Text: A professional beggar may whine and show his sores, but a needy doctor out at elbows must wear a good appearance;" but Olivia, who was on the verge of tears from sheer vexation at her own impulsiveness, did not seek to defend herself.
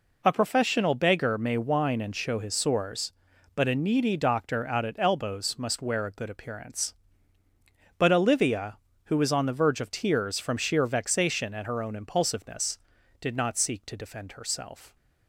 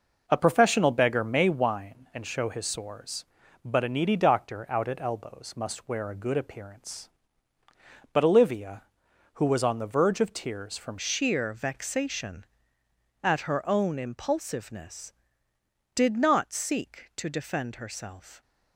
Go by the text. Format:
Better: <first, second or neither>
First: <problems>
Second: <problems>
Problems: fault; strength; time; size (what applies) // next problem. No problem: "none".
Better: first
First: none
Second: changes voice at "sheer"; from 10.9 s on; 7.5 s long